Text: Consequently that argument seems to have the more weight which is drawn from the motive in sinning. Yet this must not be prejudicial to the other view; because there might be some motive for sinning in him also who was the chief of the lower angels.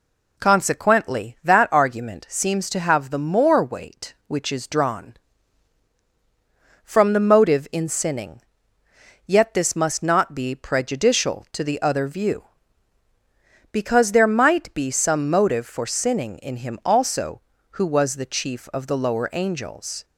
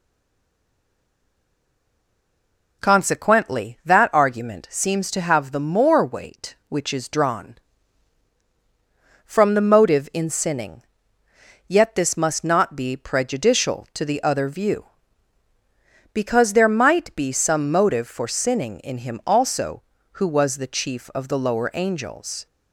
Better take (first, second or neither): first